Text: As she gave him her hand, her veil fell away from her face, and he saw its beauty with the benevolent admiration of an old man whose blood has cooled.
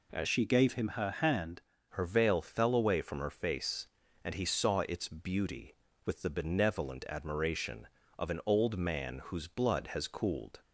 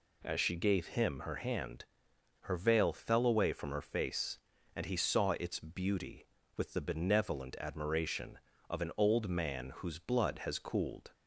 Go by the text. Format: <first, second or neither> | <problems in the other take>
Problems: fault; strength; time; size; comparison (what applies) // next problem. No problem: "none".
second | changes voice from "she" to "hand"; from 0.2 to 1.6 s; 1.4 s long